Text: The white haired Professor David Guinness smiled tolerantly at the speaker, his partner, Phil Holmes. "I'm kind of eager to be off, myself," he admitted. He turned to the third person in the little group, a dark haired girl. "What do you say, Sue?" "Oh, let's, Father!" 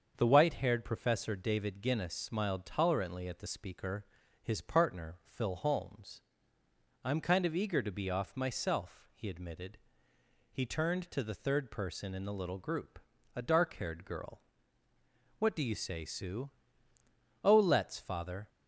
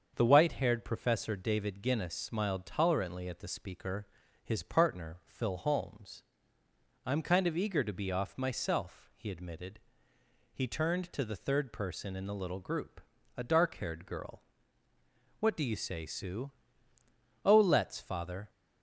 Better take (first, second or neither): neither